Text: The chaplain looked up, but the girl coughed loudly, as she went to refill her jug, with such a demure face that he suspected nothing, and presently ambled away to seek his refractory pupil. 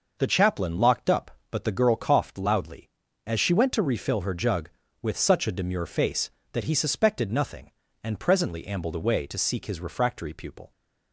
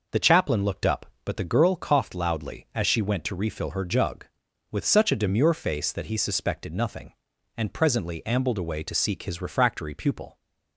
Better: second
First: says "locked" for "looked"; at 0.7 s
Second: none

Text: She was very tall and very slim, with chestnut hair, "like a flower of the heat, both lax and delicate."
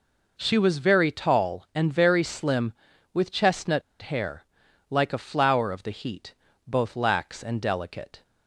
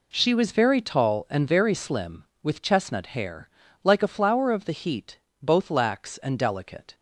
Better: second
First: pauses between "chestnut" and "hair"; slight; at 3.8 s; 0.21 s long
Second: none

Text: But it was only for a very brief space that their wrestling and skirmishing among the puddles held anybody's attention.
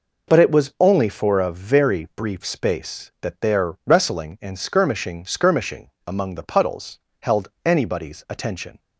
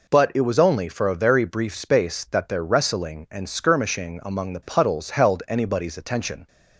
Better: second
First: says "skirmishing" twice; at 5.2 s // pauses between "puddles" and "held"; slight; at 6.9 s; 0.22 s long // pauses between "held" and "anybody's"; slight; at 7.4 s; 0.18 s long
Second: none

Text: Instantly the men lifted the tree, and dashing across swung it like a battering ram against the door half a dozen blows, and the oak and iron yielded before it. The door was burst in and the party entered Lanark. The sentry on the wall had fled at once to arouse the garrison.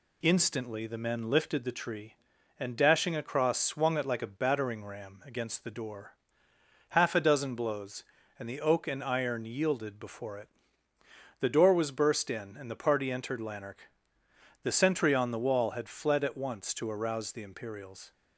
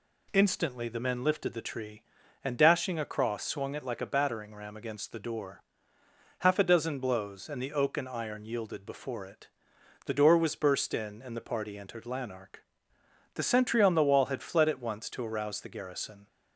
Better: second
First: pauses between "door" and "half"; noticeable; at 6.1 s; 0.76 s long // says "imperials" for "garrison"; at 17.4 s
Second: pauses between "door" and "half"; noticeable; at 5.6 s; 0.82 s long

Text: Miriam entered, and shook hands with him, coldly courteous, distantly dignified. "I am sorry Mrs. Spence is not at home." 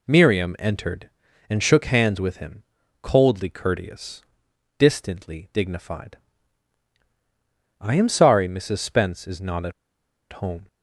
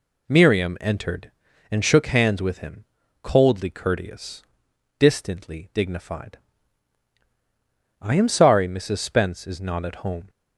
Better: second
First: pauses between "at" and "home"; noticeable; at 9.7 s; 0.60 s long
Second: none

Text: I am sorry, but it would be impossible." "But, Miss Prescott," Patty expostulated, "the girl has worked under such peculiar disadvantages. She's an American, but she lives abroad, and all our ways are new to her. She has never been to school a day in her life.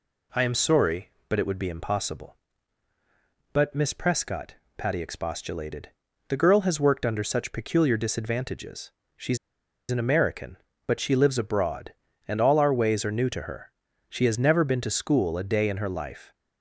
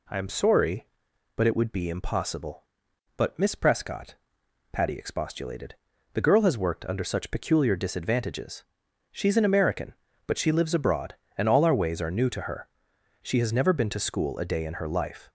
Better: second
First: pauses between "She's" and "an"; noticeable; at 9.3 s; 0.53 s long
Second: none

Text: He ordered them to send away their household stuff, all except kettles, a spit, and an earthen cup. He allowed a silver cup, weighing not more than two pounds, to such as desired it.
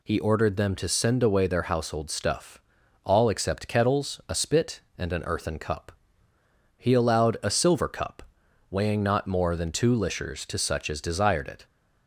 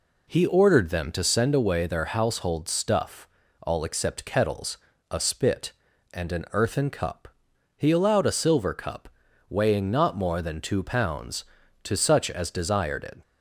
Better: second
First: says "lishers" for "pounds"; at 9.9 s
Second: none

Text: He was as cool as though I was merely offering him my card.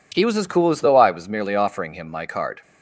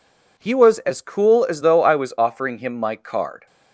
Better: first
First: none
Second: skips "merely"; at 2.1 s

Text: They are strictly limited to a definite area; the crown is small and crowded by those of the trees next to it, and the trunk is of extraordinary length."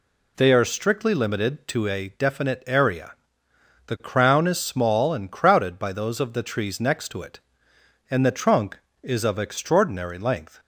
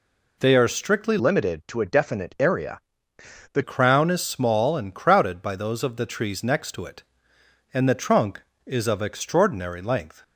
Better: first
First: none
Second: changes voice from "limited" to "the"; from 1.1 to 3.6 s; 2.5 s long

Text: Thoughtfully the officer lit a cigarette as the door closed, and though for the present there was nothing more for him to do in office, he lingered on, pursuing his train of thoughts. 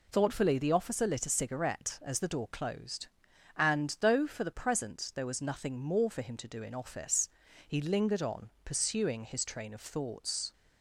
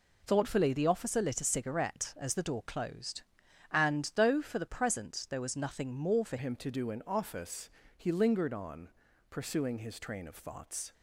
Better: first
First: none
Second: changes voice at "him"; from 6.3 s on; 4.6 s long

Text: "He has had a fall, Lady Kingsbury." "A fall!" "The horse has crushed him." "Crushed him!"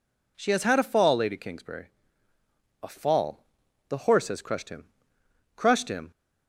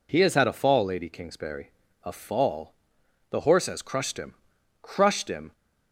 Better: second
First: says "She" for "He"; at 0.3 s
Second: none

